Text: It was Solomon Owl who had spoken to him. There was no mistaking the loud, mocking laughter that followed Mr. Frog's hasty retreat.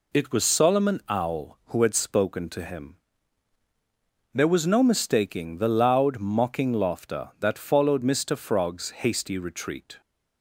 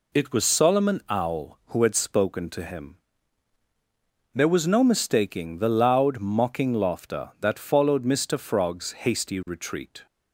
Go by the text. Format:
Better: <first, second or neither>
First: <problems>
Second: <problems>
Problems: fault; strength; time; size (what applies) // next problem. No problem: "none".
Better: neither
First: none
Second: none